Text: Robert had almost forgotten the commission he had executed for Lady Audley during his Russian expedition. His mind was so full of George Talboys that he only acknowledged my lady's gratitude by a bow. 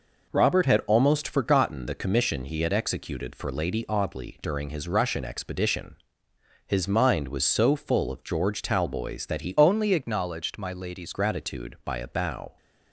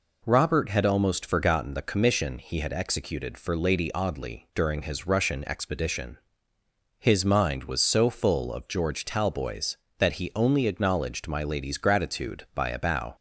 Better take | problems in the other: second | changes voice from "only" to "lady's"; from 9.5 to 11.1 s; 1.6 s long

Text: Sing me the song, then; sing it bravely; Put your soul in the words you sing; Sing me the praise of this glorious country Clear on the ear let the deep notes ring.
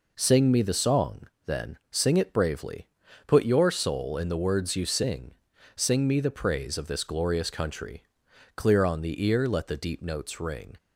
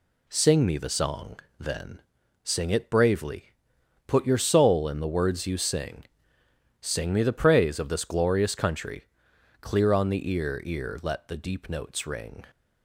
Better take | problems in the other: first | pauses between "country" and "Clear"; noticeable; at 9.0 s; 0.58 s long; noticeable in the first // says "ear" twice; at 10.6 s

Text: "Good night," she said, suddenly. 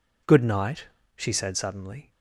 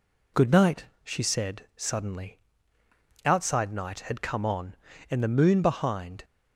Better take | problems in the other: first | goes on to say "Outside night had come on and the moon behind"; strong; from 3.2 s on; 3.0 s long

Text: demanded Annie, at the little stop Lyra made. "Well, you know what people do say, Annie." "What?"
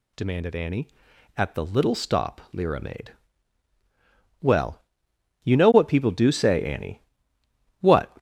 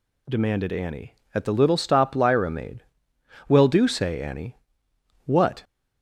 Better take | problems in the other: first | skips "you know what people"; at 3.6 s

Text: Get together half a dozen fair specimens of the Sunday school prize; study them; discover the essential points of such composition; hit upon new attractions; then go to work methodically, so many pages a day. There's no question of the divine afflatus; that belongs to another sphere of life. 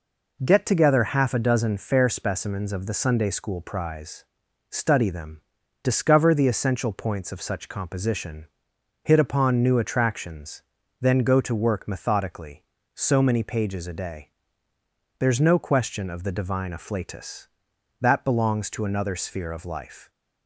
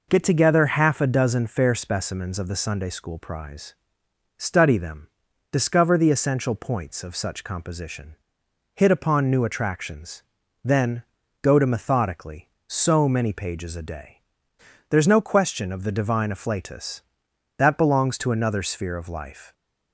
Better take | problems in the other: first | pauses between "then" and "go"; at 11.0 s; 0.40 s long // skips "work"; at 11.6 s

